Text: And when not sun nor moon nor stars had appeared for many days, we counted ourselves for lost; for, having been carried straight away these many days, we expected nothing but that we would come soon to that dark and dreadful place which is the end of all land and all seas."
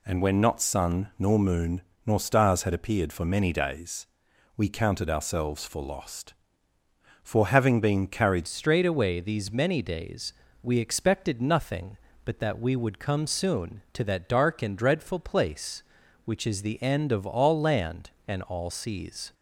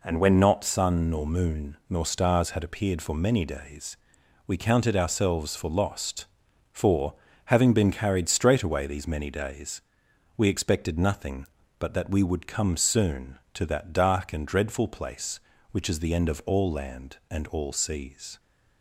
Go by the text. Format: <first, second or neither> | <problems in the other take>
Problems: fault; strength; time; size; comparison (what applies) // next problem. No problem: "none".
second | pauses between "moon" and "nor"; slight; at 1.8 s; 0.24 s long // changes voice at "straight"; from 8.4 s on; 10.9 s long